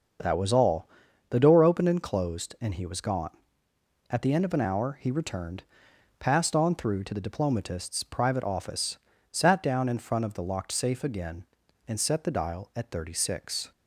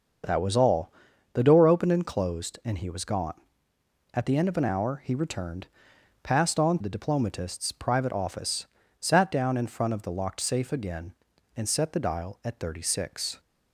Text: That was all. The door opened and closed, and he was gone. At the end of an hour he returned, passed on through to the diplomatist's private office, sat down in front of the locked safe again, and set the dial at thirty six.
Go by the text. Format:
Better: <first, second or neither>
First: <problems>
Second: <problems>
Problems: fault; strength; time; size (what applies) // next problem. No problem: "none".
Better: first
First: starts louder than the rest; until 1.6 s; 6.5 dB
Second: starts louder than the rest; until 1.6 s; 6.5 dB // skips "through to"; at 6.8 s